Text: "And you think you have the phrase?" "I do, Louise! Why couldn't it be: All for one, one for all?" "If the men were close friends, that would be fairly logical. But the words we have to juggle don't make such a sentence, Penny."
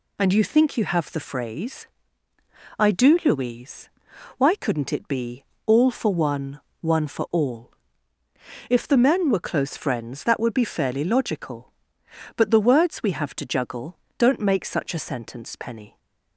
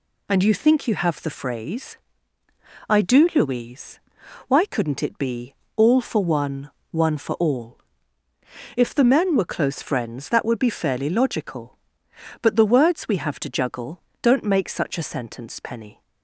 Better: neither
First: pauses between "juggle" and "don't"; slight; at 13.9 s; 0.22 s long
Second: pauses between "juggle" and "don't"; slight; at 13.9 s; 0.22 s long

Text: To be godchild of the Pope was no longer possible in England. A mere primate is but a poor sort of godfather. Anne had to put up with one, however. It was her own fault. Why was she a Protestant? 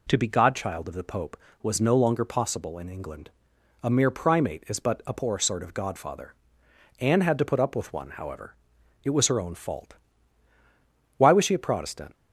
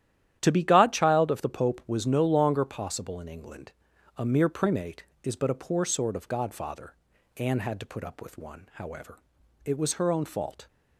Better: first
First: none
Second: starts louder than the rest; strong; until 1.4 s; 11 dB // stops before "Why was she a Protestant"; at 10.6 s

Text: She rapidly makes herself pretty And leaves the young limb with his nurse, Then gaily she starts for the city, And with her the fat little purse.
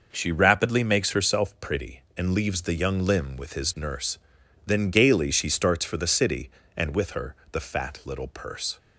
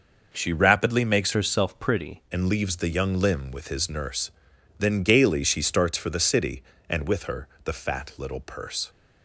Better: first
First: pauses between "her" and "the"; slight; at 7.3 s; 0.18 s long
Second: changes voice from "herself" to "pretty"; from 1.3 to 2.2 s; 0.9 s long // pauses between "her" and "the"; slight; at 7.4 s; 0.18 s long

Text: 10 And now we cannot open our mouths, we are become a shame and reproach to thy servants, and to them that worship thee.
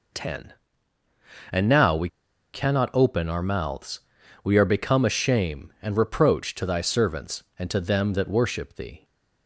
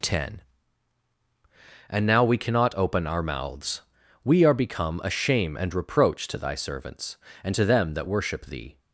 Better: second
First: pauses between "we" and "cannot"; noticeable; at 2.0 s; 0.46 s long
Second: none

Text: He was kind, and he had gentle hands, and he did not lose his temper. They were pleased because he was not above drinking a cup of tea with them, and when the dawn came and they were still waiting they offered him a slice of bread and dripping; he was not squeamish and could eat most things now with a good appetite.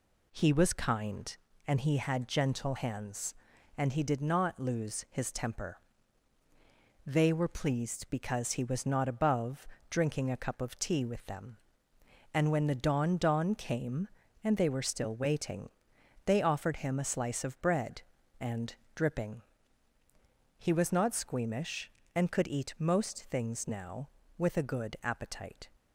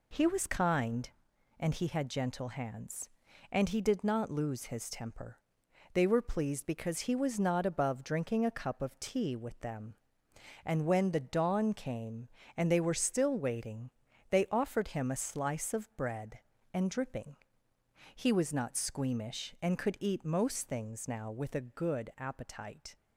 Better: second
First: pauses between "above" and "drinking"; slight; at 9.6 s; 0.22 s long // says "dawn" twice; at 13.1 s // pauses between "waiting" and "they"; noticeable; at 15.6 s; 0.56 s long // pauses between "and" and "dripping"; slight; at 18.7 s; 0.22 s long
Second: pauses between "waiting" and "they"; at 13.8 s; 0.40 s long

